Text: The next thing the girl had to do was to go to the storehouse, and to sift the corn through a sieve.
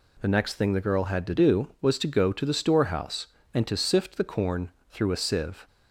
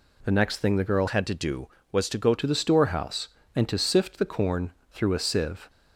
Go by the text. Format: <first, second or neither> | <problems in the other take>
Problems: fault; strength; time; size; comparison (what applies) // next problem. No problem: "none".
first | changes voice from "had" to "go"; from 1.0 to 2.3 s; 1.3 s long // pauses between "corn" and "through"; slight; at 4.7 s; 0.18 s long; slight in the first